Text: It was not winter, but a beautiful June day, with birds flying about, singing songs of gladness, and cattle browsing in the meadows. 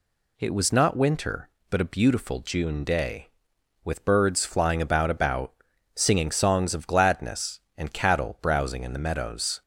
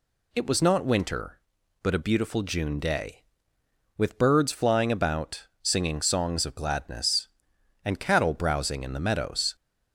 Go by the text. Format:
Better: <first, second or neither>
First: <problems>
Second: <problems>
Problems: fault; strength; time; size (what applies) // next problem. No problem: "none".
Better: second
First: says "about" twice; at 5.0 s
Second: none